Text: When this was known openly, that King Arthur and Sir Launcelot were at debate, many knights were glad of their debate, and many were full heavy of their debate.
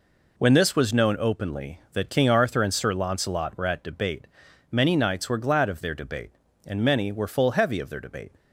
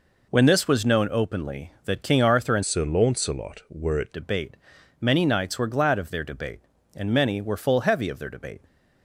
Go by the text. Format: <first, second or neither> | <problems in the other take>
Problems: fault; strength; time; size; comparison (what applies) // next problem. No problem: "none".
first | changes voice from "Sir" to "at"; from 2.6 to 4.1 s; 1.5 s long